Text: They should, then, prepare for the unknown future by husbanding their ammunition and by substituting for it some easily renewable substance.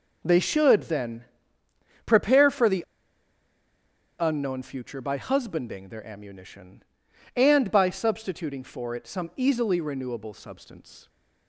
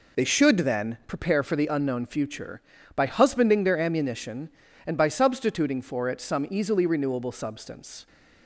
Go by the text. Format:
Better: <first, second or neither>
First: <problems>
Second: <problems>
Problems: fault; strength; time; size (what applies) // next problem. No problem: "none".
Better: second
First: pauses between "the" and "unknown"; strong; at 2.8 s; 1.3 s long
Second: none